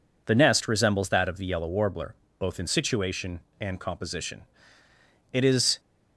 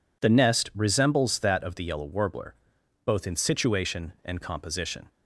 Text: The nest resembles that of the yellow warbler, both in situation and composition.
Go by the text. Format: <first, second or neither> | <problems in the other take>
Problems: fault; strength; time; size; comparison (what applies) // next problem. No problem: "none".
second | goes on to say "It is"; slight; from 5.3 s on; 0.48 s long